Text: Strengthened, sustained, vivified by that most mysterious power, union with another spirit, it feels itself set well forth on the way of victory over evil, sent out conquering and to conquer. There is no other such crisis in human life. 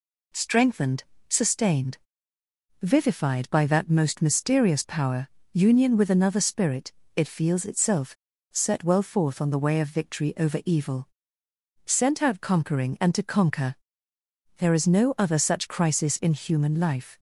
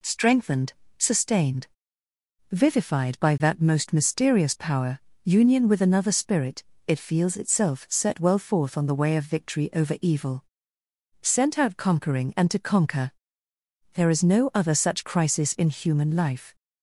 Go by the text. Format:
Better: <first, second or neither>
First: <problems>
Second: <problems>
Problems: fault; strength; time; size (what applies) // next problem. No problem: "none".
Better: second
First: pauses between "itself" and "set"; at 8.1 s; 0.39 s long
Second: none